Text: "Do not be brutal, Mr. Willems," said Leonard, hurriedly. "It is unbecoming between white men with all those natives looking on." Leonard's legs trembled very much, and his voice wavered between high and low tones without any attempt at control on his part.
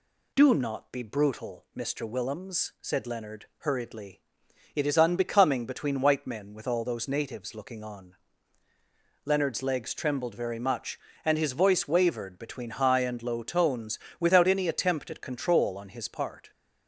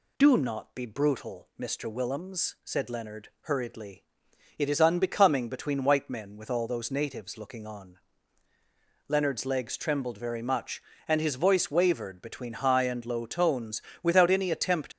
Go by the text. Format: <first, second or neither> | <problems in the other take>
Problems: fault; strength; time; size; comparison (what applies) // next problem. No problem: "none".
first | pauses between "tones" and "without"; slight; at 13.8 s; 0.22 s long; slight in the first // stops before "at control on his part"; at 14.9 s